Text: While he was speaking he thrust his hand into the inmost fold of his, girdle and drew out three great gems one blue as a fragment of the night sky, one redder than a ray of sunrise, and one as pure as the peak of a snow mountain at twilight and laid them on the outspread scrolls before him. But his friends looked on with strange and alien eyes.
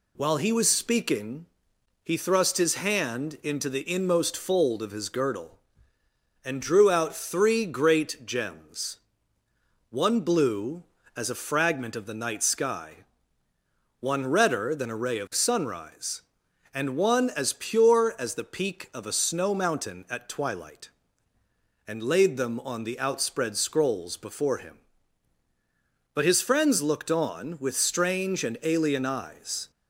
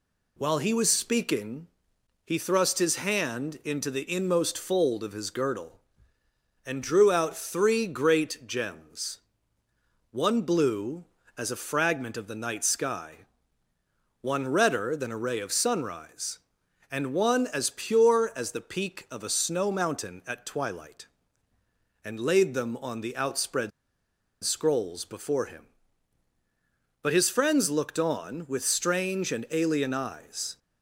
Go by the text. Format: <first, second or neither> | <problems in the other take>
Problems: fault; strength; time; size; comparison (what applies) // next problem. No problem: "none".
first | pauses between "speaking" and "he"; noticeable; at 1.6 s; 0.58 s long; noticeable in the first // pauses between "gems" and "one"; noticeable; at 9.1 s; 0.94 s long; noticeable in the first // pauses between "outspread" and "scrolls"; noticeable; at 23.7 s; 0.73 s long